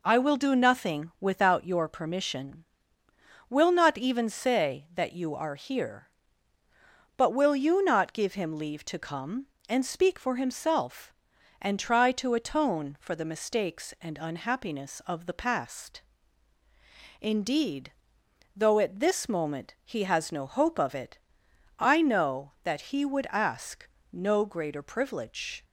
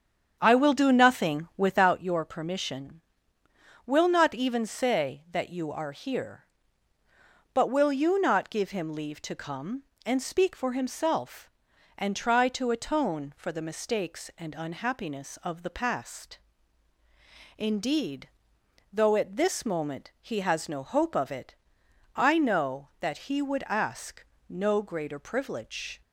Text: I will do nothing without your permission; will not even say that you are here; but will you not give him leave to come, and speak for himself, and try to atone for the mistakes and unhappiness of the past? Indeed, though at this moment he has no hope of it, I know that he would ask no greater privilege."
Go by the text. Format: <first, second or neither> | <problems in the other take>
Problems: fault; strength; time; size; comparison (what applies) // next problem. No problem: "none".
first | starts louder than the rest; strong; until 2.0 s; 8 dB // pauses between "ask" and "no"; slight; at 24.2 s; 0.24 s long; slight in the first